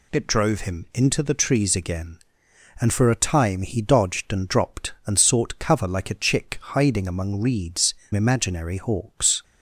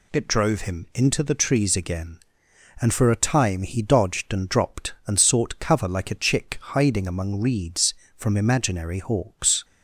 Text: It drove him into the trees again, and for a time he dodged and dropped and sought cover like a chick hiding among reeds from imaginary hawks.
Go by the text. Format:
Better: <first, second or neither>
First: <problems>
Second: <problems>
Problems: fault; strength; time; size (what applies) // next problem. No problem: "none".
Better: second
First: pauses between "chick" and "hiding"; slight; at 6.5 s; 0.16 s long // skips "from"; at 8.0 s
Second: pauses between "chick" and "hiding"; slight; at 6.5 s; 0.16 s long